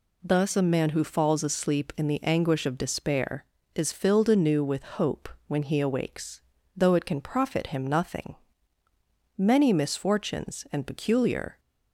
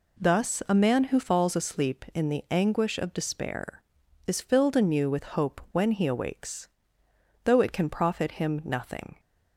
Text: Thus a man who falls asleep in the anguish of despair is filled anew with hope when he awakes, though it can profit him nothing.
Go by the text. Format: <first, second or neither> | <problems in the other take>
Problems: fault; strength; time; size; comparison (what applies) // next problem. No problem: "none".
second | pauses between "hope" and "when"; slight; at 5.2 s; 0.18 s long // goes on to say "Many misfortunes and peculiar"; strong; from 9.3 s on; 2.2 s long